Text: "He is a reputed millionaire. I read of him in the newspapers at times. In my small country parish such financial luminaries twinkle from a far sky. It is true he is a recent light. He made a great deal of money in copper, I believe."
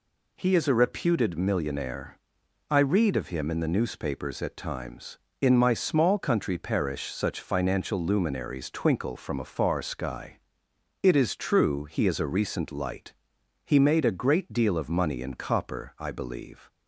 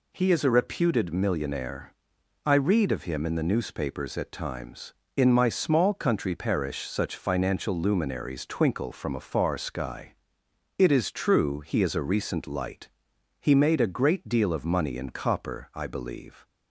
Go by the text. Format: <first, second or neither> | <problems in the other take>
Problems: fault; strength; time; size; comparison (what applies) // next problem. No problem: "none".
neither | none